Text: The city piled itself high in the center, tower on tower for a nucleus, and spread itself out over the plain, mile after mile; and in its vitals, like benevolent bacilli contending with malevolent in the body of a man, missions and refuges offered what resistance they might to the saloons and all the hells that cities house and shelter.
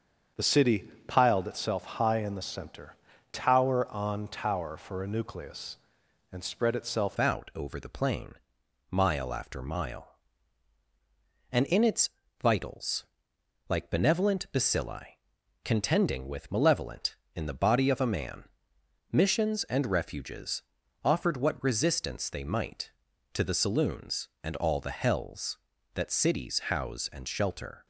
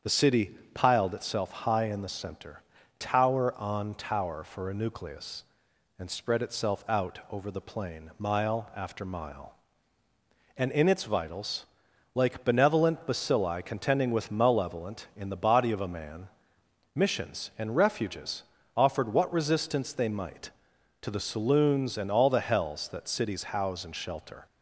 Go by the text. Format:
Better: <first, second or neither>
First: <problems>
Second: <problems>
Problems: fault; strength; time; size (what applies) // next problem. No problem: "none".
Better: second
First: starts louder than the rest; until 1.5 s; 7 dB // pauses between "city" and "piled"; slight; at 0.8 s; 0.20 s long // changes voice at "out"; from 7.1 s on; 20.7 s long // pauses between "its" and "vitals"; slight; at 12.0 s; 0.32 s long // pauses between "bacilli" and "contending"; noticeable; at 15.1 s; 0.46 s long // pauses between "refuges" and "offered"; at 20.6 s; 0.44 s long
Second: starts louder than the rest; strong; until 1.2 s; 7.5 dB // pauses between "city" and "piled"; slight; at 0.5 s; 0.20 s long // pauses between "refuges" and "offered"; slight; at 18.4 s; 0.32 s long